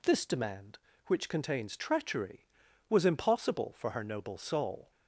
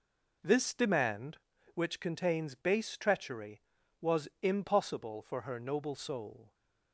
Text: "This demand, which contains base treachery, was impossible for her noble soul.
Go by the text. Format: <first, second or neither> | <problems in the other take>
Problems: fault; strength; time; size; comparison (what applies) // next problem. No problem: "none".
second | skips "base"; at 1.7 s